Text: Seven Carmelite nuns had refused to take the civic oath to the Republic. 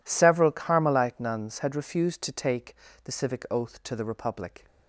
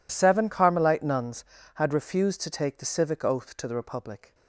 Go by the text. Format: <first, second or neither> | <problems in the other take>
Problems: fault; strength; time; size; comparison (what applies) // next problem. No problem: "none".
second | says "Several" for "Seven"; at 0.0 s // pauses between "take" and "the"; slight; at 2.7 s; 0.30 s long